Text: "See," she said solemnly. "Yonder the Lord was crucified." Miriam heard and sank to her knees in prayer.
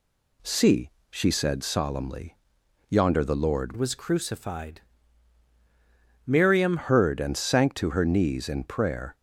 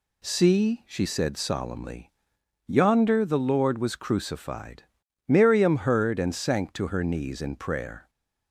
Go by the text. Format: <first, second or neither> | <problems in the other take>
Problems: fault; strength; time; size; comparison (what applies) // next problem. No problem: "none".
second | changes voice from "was" to "Miriam"; from 3.7 to 6.7 s; 3.0 s long